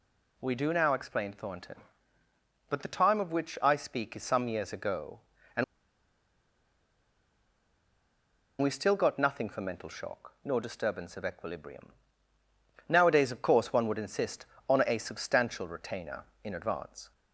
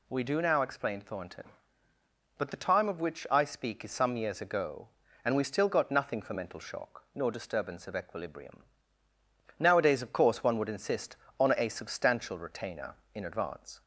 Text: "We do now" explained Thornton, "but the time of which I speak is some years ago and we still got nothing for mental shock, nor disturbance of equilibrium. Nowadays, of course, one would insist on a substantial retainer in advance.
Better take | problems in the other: second | pauses between "and" and "we"; strong; at 5.6 s; 2.9 s long

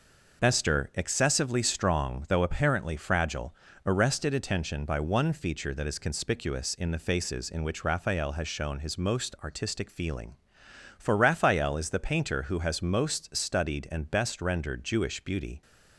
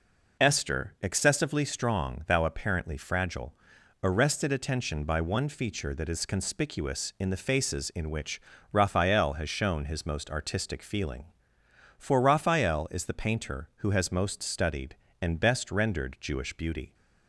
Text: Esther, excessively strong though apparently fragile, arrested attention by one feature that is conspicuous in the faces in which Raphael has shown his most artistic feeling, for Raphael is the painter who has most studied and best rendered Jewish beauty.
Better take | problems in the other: first | says "thou" for "though"; at 2.2 s // pauses between "which" and "Raphael"; slight; at 8.4 s; 0.30 s long

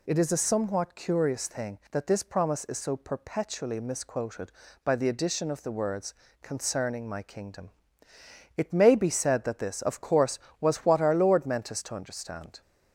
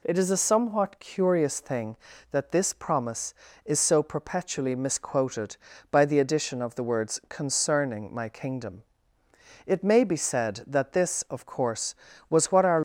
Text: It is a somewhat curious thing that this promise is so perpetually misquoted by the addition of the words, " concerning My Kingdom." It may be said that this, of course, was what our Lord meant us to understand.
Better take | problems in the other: first | stops before "Lord meant us to understand"; at 12.7 s

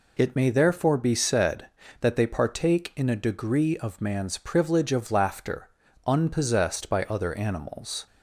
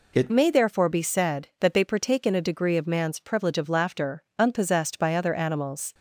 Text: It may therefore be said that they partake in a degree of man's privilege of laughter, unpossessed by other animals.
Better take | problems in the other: first | changes voice at "may"; from 0.3 s on; 5.6 s long

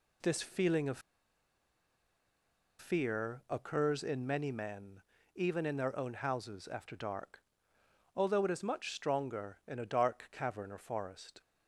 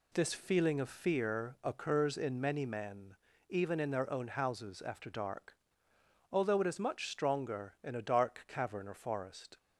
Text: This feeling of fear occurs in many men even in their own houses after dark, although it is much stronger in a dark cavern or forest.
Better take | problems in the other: second | pauses between "of" and "fear"; strong; at 0.9 s; 1.7 s long // pauses between "men" and "even"; slight; at 5.0 s; 0.34 s long; slight in the second

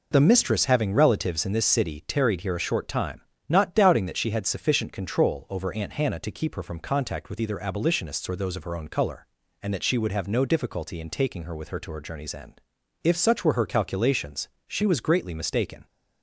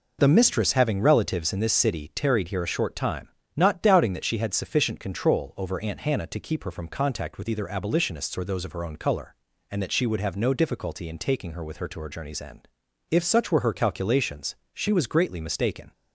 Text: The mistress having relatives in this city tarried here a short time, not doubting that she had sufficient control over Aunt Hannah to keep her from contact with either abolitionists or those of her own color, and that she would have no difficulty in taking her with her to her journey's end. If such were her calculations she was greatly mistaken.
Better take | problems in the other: neither | pauses between "calculations" and "she"; slight; the same in both

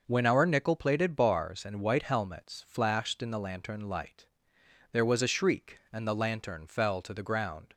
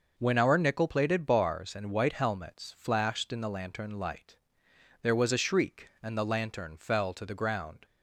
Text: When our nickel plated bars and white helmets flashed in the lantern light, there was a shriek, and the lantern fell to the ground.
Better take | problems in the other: neither | none

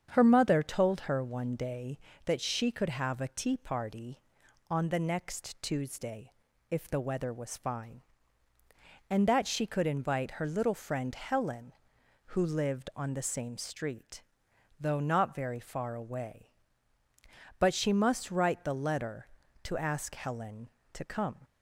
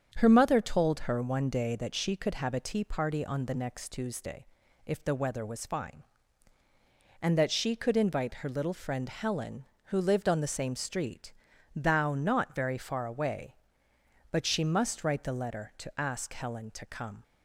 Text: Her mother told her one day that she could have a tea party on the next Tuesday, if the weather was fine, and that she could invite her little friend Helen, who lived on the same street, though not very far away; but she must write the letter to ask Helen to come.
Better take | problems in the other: first | starts louder than the rest; strong; until 1.1 s; 7.5 dB; strong in the first // says "thou" for "though"; at 11.7 s

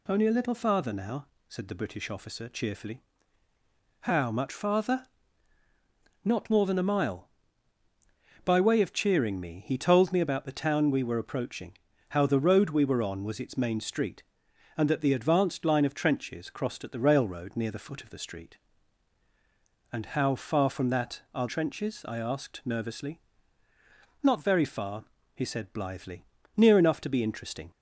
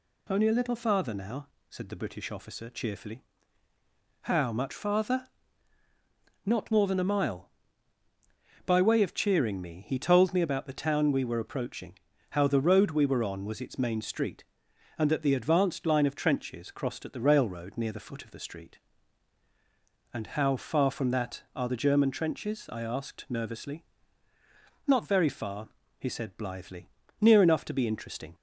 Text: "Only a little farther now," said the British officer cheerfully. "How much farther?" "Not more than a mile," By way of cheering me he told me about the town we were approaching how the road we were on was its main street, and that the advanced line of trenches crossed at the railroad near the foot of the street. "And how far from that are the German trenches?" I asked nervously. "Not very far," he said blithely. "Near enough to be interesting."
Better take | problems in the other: second | pauses between "approaching" and "how"; slight; at 11.7 s; 0.34 s long; slight in the second // skips "the German"; at 21.4 s

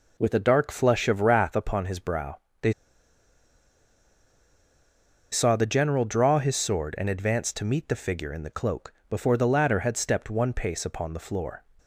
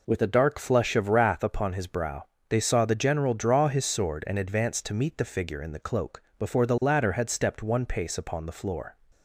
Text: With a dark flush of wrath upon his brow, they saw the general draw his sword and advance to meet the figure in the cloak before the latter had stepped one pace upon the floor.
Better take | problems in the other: second | pauses between "they" and "saw"; strong; at 2.7 s; 2.5 s long // pauses between "cloak" and "before"; slight; at 8.9 s; 0.16 s long; slight in the second

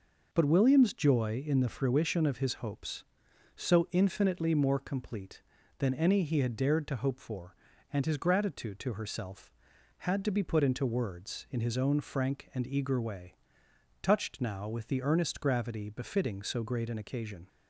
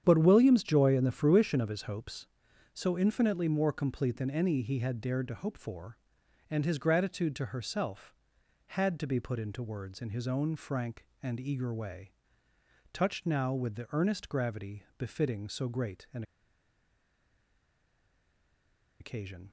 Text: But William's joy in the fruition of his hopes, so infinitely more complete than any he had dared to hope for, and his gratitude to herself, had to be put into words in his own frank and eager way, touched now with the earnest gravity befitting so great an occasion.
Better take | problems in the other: first | starts louder than the rest; strong; until 1.0 s; 9 dB // pauses between "gravity" and "befitting"; slight; at 14.8 s; 0.16 s long // pauses between "an" and "occasion"; strong; at 16.2 s; 2.7 s long

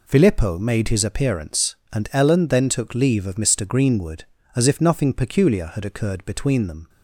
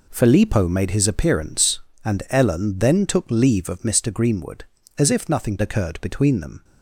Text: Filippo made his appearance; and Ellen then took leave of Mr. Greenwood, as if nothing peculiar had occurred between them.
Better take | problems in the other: first | skips "peculiar had"; at 5.5 s

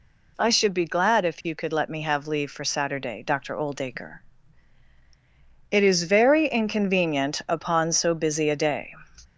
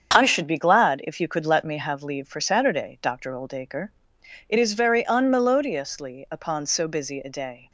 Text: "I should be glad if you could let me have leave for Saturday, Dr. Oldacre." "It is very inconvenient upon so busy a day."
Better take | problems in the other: first | starts louder than the rest; strong; until 1.1 s; 7.5 dB // says "unmelodiously" for "inconvenient"; at 5.0 s

